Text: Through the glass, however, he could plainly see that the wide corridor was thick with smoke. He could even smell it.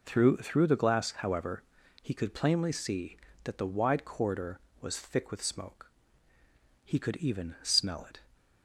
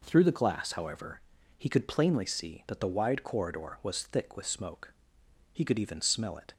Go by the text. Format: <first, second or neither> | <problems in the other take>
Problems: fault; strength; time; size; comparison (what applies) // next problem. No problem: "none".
second | says "Through" twice; at 0.3 s